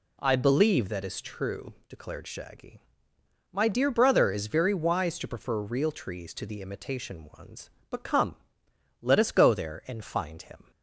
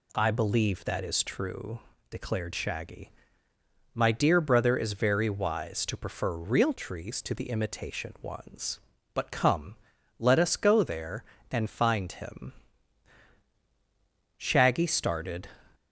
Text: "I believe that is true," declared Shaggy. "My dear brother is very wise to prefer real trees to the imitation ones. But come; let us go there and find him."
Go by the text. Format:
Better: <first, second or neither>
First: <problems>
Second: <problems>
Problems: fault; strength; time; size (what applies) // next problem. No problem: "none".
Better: first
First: none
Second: goes on to say "Shaggy started"; noticeable; from 14.3 s on; 1.1 s long